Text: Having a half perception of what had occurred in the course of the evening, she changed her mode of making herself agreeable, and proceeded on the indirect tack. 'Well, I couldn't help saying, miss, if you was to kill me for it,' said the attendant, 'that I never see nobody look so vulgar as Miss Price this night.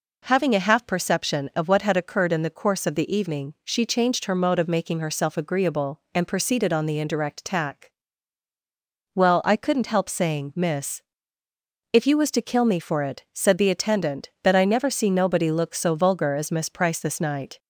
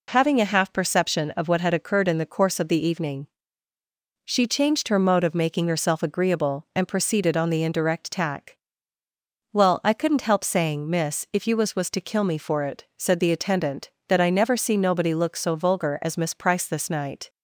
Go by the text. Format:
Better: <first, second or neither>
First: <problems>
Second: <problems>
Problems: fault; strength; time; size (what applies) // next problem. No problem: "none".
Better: first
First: none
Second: says "was" twice; at 11.7 s